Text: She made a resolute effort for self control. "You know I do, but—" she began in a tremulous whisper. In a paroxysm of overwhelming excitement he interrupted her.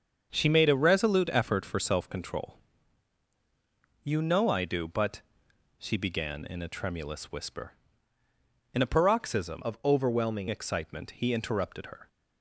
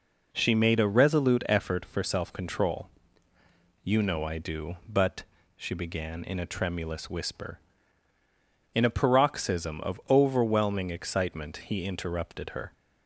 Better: second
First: starts louder than the rest; until 1.3 s; 7 dB // changes voice from "of" to "overwhelming"; from 9.6 to 10.4 s; 0.8 s long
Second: none

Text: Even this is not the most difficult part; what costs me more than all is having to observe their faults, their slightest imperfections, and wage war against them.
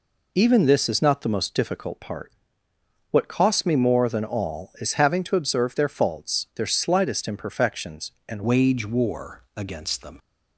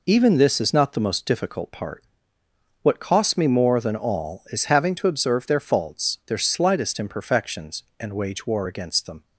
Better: second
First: changes voice at "wage"; from 8.4 s on; 1.7 s long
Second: none

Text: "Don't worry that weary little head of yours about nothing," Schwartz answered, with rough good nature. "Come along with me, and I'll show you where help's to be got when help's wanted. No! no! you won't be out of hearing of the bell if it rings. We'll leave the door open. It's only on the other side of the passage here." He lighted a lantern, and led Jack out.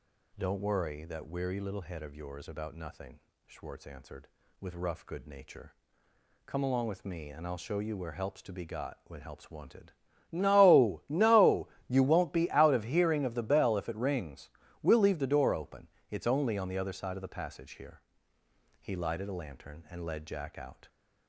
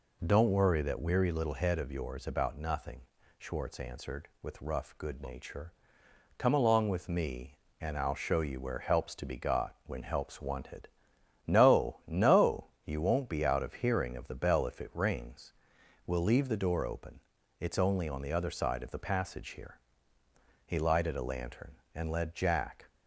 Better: first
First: none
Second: stops before "out"; at 22.8 s

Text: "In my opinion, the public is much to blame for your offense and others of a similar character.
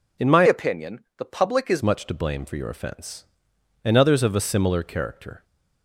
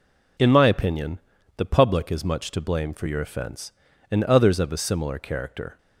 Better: second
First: changes voice from "opinion" to "is"; from 0.4 to 1.8 s; 1.4 s long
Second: none

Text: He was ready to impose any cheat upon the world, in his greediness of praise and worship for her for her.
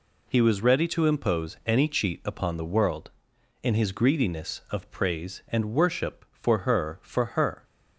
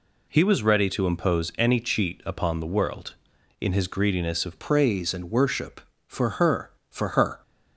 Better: first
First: none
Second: changes voice at "praise"; from 4.5 s on; 2.9 s long

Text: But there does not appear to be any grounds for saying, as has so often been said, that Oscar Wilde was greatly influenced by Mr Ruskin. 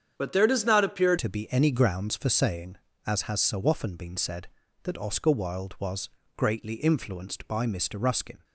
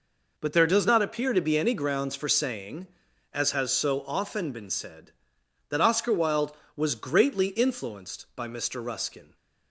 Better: second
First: starts louder than the rest; strong; until 1.1 s; 8 dB // changes voice at "to"; from 1.1 s on; 7.3 s long // pauses between "was" and "greatly"; slight; at 6.0 s; 0.26 s long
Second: none

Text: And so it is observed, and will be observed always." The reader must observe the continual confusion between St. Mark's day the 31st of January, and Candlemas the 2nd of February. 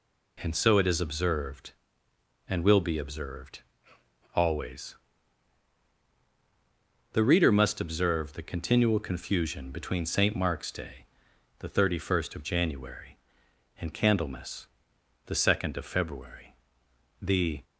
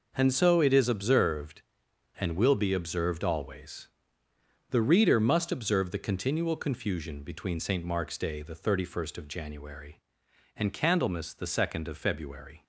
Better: second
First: pauses between "observed" and "always"; noticeable; at 3.6 s; 0.74 s long // pauses between "day" and "the"; noticeable; at 11.0 s; 0.51 s long // pauses between "Candlemas" and "the"; noticeable; at 14.6 s; 0.58 s long // goes on to say "The"; slight; from 17.1 s on; 0.44 s long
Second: none

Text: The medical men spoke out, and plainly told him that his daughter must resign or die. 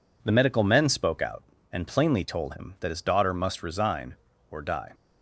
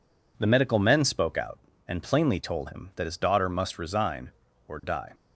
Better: neither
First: none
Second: none

